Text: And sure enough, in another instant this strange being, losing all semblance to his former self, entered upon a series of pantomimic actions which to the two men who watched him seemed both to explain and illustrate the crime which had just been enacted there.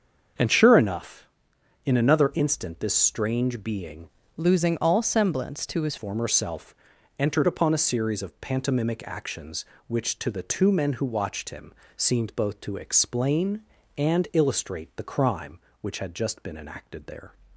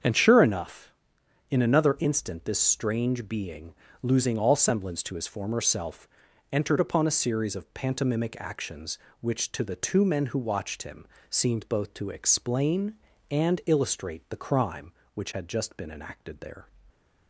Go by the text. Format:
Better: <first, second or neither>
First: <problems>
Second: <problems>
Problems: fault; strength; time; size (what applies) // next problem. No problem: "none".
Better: second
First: starts louder than the rest; until 1.9 s; 7 dB // changes voice from "losing" to "his"; from 4.3 to 5.9 s; 1.6 s long // pauses between "him" and "seemed"; slight; at 11.7 s; 0.24 s long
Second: starts louder than the rest; strong; until 1.6 s; 7 dB // pauses between "him" and "seemed"; slight; at 11.0 s; 0.24 s long